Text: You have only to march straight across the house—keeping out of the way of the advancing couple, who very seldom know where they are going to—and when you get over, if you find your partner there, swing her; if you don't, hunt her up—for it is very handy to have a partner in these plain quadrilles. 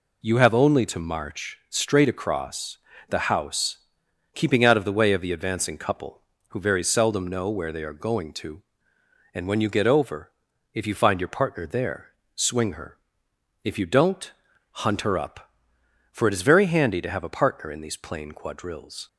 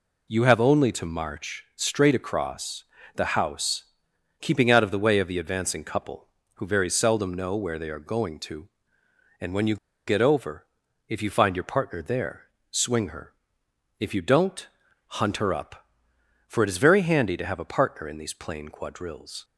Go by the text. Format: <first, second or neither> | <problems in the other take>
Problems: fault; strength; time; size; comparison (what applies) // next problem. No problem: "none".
first | pauses between "across" and "the"; slight; at 2.8 s; 0.32 s long; slight in the first // pauses between "you" and "get"; slight; at 9.7 s; 0.31 s long